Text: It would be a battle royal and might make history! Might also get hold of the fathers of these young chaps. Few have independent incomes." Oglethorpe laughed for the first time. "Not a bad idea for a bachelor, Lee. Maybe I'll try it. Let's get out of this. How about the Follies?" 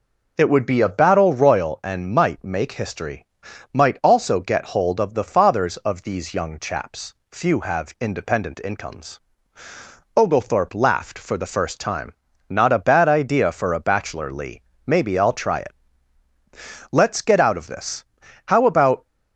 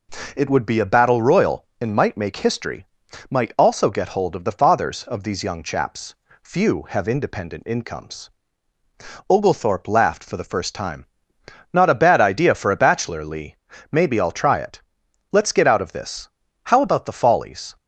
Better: second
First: stops before "the Follies"; at 19.0 s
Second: none

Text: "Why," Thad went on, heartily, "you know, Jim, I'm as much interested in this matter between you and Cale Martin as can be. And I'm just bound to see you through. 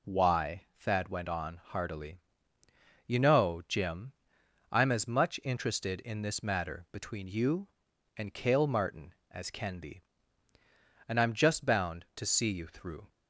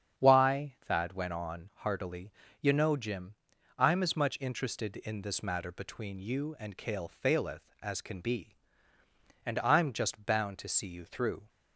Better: first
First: none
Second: starts louder than the rest; strong; until 1.2 s; 8 dB // says "Faileth" for "Martin"; at 7.0 s

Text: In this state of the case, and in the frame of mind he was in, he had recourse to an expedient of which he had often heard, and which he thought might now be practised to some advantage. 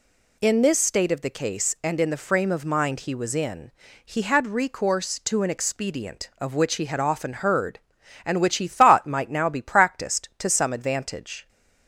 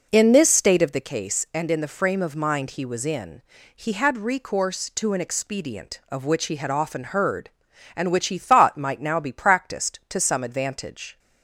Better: first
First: none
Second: starts louder than the rest; noticeable; until 1.1 s; 4.5 dB

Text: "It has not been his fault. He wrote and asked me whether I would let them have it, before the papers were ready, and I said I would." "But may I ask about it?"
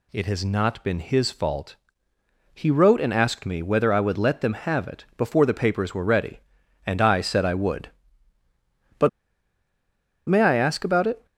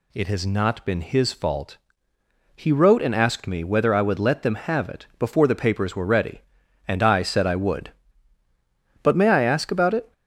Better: second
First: pauses between "But" and "may"; at 9.0 s; 1.2 s long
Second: none

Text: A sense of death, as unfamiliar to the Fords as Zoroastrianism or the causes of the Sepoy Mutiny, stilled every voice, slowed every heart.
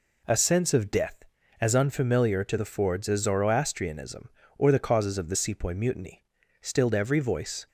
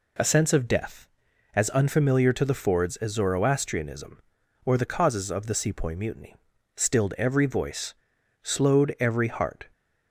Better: second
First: stops before "slowed every heart"; at 7.6 s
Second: none

